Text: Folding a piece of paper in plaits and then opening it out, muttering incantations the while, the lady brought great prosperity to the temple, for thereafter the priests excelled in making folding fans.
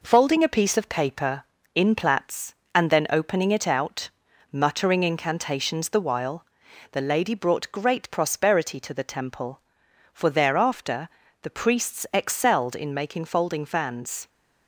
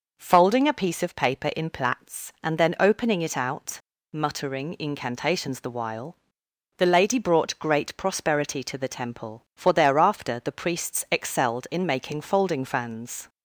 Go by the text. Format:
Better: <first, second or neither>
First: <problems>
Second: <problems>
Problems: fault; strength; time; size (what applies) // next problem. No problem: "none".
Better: second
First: gets quieter; noticeable; throughout; 4 dB // pauses between "thereafter" and "the"; slight; at 11.0 s; 0.34 s long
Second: none